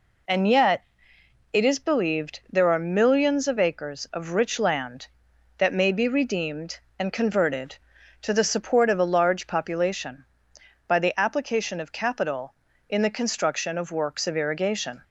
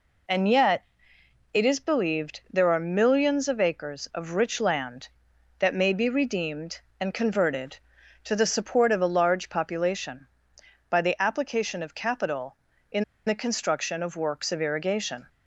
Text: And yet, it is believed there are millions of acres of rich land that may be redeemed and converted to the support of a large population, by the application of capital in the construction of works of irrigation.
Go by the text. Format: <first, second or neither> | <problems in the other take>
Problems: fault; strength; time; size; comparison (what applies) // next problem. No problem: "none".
first | pauses between "in" and "the"; slight; at 13.0 s; 0.22 s long